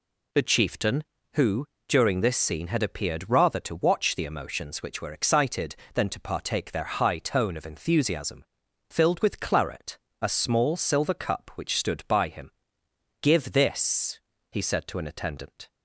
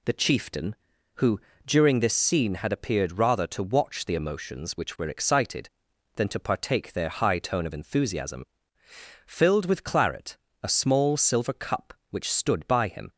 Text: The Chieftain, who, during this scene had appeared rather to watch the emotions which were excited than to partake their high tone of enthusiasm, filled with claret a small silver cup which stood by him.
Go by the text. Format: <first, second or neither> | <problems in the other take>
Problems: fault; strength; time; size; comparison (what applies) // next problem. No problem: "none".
second | pauses between "claret" and "a"; slight; at 9.9 s; 0.24 s long; slight in the second // goes on to say "Give this he said to an attendant"; strong; from 13.2 s on; 2.4 s long